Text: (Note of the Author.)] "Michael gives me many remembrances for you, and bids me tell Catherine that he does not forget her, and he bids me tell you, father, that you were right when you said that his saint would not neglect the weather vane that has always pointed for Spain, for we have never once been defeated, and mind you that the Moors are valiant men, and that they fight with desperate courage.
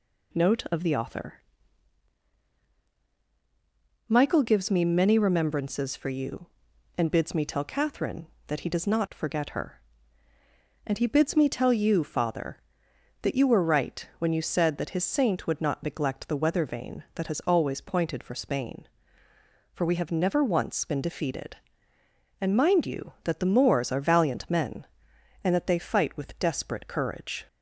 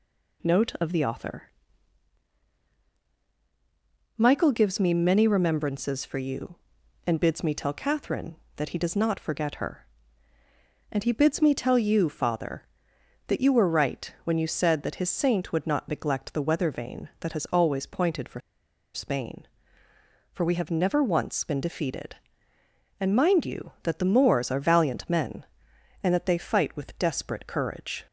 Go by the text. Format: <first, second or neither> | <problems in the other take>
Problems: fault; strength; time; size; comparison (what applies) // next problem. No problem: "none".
first | pauses between "for" and "Spain"; noticeable; at 18.3 s; 0.54 s long